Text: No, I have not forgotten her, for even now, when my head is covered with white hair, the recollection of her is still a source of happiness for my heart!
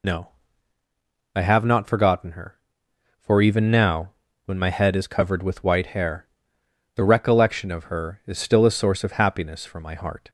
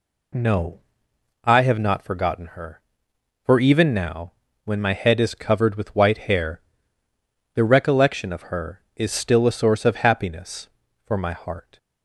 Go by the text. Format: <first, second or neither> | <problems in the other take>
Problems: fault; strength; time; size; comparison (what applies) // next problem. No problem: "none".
second | loses the start of "No"; at 0.0 s; 45 ms